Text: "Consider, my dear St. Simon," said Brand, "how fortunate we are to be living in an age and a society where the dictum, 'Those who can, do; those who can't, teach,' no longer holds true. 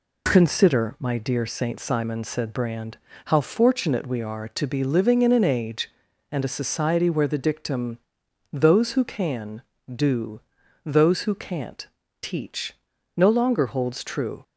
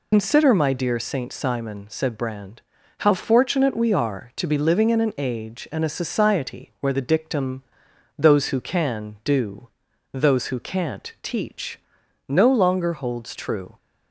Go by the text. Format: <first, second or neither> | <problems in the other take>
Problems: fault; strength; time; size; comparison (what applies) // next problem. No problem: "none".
first | loses the start of "Consider"; at 0.1 s; 100 ms